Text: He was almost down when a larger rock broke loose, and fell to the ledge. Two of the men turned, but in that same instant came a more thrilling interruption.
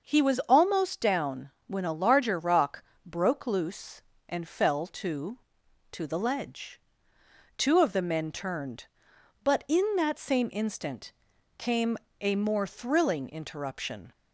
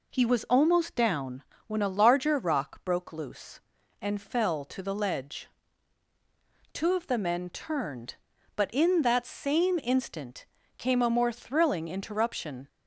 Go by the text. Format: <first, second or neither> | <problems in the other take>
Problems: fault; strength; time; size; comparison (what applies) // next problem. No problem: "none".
second | starts louder than the rest; until 1.1 s; 6.5 dB // pauses between "down" and "when"; slight; at 1.5 s; 0.16 s long; slight in the second // pauses between "rock" and "broke"; slight; at 2.8 s; 0.22 s long // says "to" twice; at 5.9 s // pauses between "instant" and "came"; at 11.1 s; 0.44 s long; slight in the second // pauses between "came" and "a"; slight; at 11.9 s; 0.22 s long